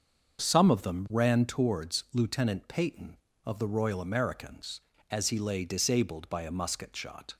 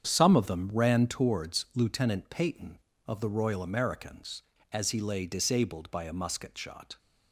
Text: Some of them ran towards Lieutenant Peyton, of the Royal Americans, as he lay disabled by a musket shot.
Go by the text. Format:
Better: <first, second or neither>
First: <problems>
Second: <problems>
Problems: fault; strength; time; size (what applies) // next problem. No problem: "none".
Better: first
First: starts louder than the rest; until 1.4 s; 7 dB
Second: gets quieter; strong; throughout; 10.5 dB // starts louder than the rest; strong; until 1.1 s; 8 dB